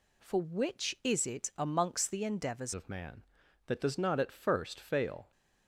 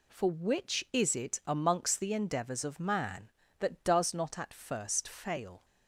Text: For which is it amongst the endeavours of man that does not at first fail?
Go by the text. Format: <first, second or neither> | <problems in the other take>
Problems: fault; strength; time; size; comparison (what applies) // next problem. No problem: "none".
second | changes voice at "of"; from 2.7 s on; 2.6 s long